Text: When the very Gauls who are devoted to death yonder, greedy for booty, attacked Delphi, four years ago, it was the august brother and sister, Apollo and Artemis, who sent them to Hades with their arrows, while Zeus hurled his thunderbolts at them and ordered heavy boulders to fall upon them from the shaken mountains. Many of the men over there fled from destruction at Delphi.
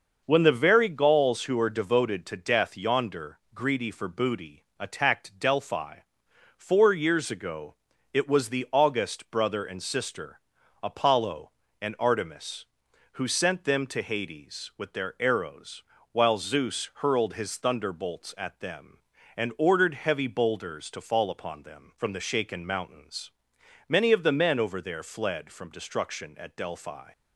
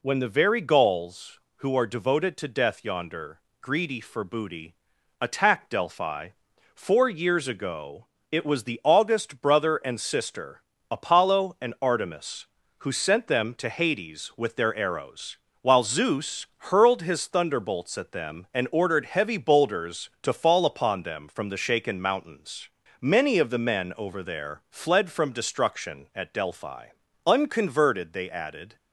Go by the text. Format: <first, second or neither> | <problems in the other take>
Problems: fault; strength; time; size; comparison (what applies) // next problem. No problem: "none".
first | goes on to say "Unconverted they added"; from 27.2 s on; 1.5 s long